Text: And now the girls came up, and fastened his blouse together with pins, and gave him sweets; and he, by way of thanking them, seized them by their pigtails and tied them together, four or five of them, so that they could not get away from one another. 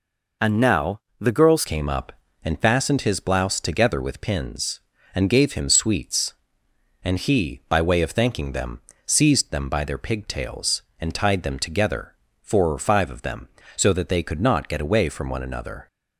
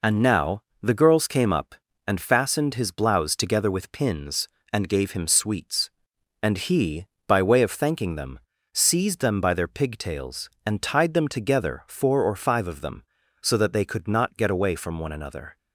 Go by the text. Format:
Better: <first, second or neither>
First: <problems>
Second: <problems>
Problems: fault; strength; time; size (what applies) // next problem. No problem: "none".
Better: second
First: pauses between "now" and "the"; slight; at 0.9 s; 0.20 s long // changes voice at "came"; from 1.6 s on; 14.2 s long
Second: pauses between "now" and "the"; slight; at 0.6 s; 0.20 s long